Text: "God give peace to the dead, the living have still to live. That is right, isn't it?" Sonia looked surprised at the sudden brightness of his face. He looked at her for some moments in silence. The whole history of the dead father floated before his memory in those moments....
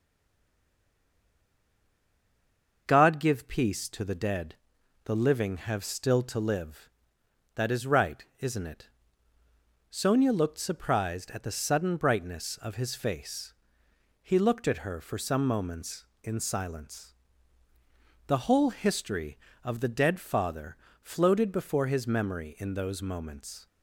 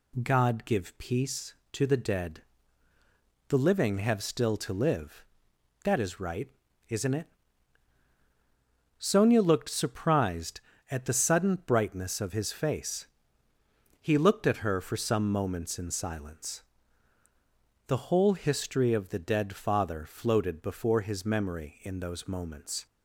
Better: second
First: stays silent before the first word; strong; until 2.8 s; 2.8 s long // starts louder than the rest; until 3.8 s; 6 dB // pauses between "father" and "floated"; slight; at 20.7 s; 0.26 s long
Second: none

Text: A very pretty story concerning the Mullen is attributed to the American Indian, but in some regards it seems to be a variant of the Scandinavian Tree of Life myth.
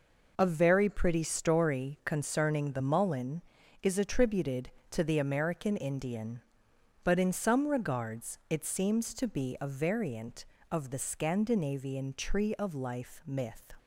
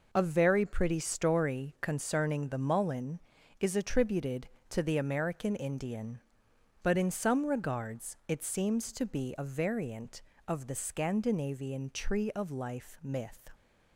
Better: neither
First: none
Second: none

